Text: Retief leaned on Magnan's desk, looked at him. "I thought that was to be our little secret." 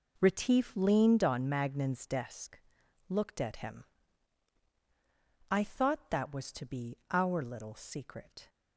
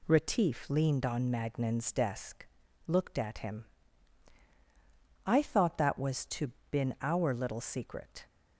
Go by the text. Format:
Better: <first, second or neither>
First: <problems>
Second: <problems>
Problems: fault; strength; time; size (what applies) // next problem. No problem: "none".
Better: first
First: none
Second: says "been" for "be"; at 6.7 s